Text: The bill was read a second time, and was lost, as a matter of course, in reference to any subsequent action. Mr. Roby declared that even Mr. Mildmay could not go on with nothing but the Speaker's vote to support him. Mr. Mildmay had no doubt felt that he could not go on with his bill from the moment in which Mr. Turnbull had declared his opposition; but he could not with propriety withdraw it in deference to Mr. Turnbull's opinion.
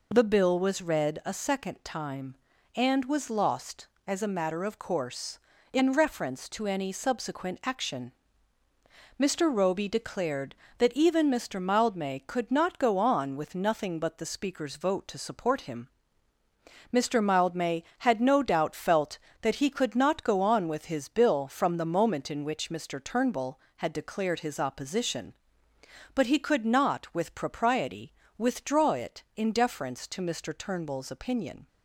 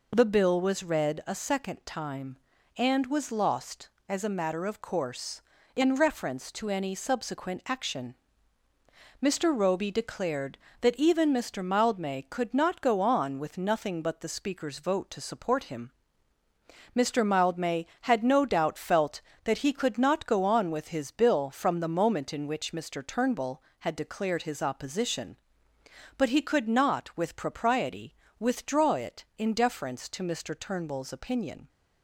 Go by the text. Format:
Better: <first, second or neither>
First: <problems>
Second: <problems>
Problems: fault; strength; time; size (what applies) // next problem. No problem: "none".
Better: neither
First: pauses between "propriety" and "withdraw"; slight; at 28.1 s; 0.26 s long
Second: pauses between "propriety" and "withdraw"; slight; at 28.1 s; 0.26 s long